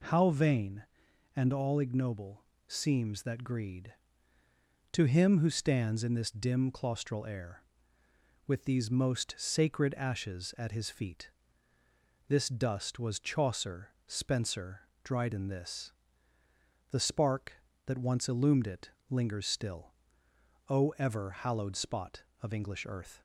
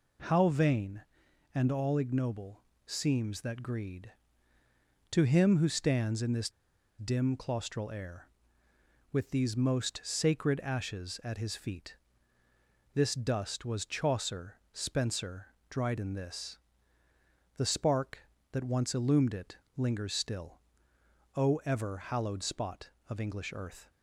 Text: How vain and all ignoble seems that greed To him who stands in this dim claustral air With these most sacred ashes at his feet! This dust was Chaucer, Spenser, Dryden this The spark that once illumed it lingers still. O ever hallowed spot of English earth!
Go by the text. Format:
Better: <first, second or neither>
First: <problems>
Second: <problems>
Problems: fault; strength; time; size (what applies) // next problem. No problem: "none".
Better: first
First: pauses between "ignoble" and "seems"; slight; at 2.4 s; 0.24 s long // pauses between "this" and "The"; at 15.9 s; 1.0 s long // pauses between "it" and "lingers"; slight; at 18.9 s; 0.20 s long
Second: pauses between "ignoble" and "seems"; slight; at 2.6 s; 0.24 s long // pauses between "this" and "dim"; noticeable; at 6.4 s; 0.49 s long // pauses between "this" and "The"; at 16.5 s; 1.0 s long // pauses between "it" and "lingers"; slight; at 19.5 s; 0.20 s long